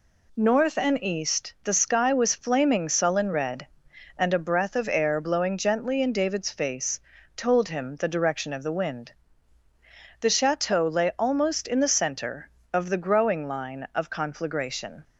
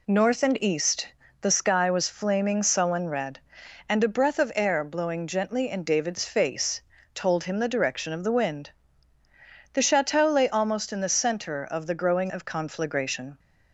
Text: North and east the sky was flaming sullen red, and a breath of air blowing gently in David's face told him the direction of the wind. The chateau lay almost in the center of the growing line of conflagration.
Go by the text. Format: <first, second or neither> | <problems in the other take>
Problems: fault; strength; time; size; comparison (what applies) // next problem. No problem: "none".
first | pauses between "east" and "the"; slight; at 1.0 s; 0.34 s long // pauses between "face" and "told"; slight; at 6.8 s; 0.32 s long; slight in the first // skips "line"; at 12.2 s